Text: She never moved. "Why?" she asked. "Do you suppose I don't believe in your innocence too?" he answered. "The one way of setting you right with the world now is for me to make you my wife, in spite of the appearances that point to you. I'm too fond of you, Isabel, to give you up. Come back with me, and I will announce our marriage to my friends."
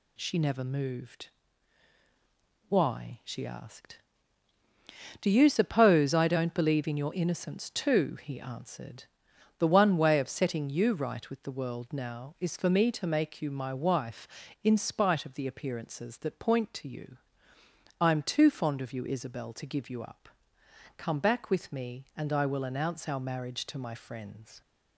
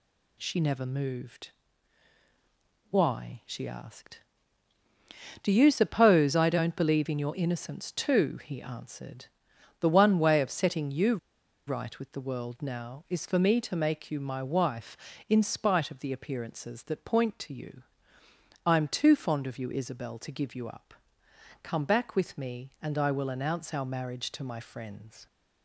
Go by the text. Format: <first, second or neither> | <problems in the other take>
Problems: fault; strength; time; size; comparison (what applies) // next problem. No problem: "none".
first | pauses between "you" and "right"; noticeable; at 11.1 s; 0.50 s long